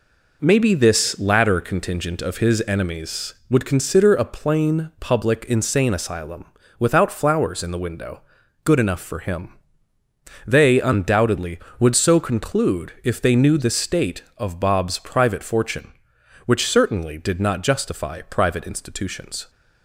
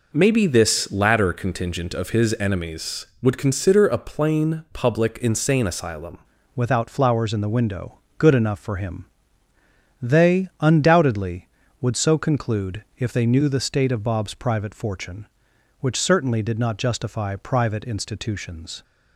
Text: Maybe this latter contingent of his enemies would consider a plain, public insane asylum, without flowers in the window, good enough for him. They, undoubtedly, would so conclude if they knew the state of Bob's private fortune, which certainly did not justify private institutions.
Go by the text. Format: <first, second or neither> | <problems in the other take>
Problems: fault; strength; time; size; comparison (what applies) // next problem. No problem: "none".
first | changes voice at "without"; from 6.5 s on; 12.3 s long